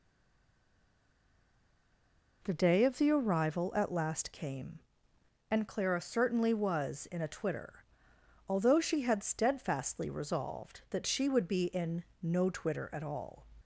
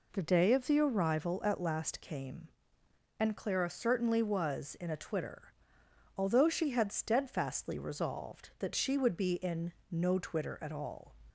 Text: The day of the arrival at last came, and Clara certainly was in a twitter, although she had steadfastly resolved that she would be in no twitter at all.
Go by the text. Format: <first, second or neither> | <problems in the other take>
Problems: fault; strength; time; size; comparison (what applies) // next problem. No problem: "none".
second | stays silent before the first word; until 2.4 s; 2.4 s long // pauses between "in" and "no"; slight; at 12.0 s; 0.18 s long; slight in the second